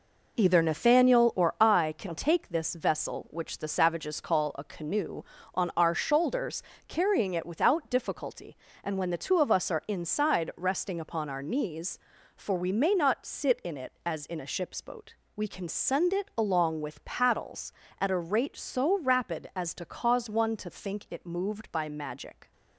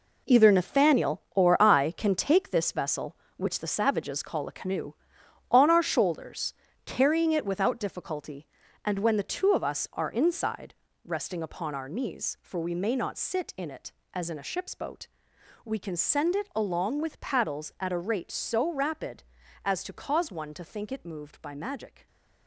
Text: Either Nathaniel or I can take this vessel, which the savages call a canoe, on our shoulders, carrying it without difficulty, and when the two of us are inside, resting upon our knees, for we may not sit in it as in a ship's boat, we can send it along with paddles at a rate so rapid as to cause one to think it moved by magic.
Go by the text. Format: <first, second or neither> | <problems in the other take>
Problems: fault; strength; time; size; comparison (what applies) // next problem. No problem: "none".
first | gets quieter; strong; throughout; 9.5 dB